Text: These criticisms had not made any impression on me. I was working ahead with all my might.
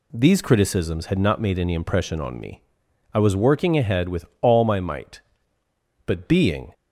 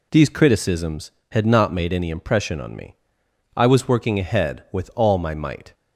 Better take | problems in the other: second | pauses between "with" and "all"; slight; at 4.2 s; 0.16 s long // goes on to say "But being"; noticeable; from 6.0 s on; 0.68 s long

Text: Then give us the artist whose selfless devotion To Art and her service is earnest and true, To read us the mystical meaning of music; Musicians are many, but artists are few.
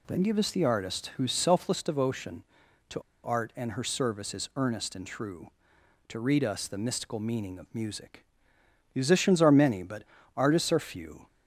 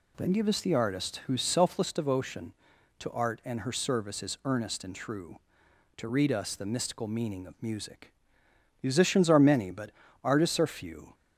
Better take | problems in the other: second | pauses between "To" and "Art"; slight; at 2.9 s; 0.23 s long // pauses between "but" and "artists"; slight; at 10.0 s; 0.32 s long; slight in the second

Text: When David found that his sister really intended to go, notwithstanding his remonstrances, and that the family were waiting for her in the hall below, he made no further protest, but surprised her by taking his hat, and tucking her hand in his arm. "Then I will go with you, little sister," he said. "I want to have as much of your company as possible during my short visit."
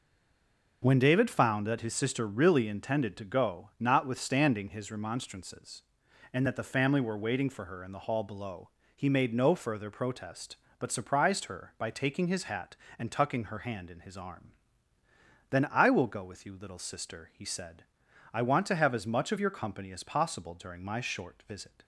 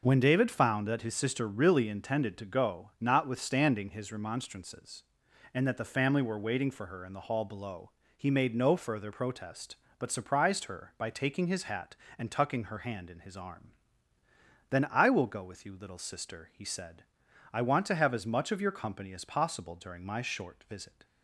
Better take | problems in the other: second | stays silent before the first word; slight; until 0.8 s; 0.8 s long

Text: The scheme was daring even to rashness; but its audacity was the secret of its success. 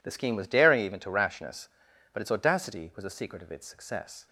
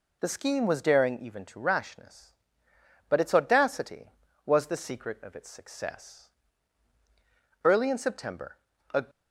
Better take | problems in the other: first | goes on to say "Early in September a"; from 7.6 s on; 1.4 s long

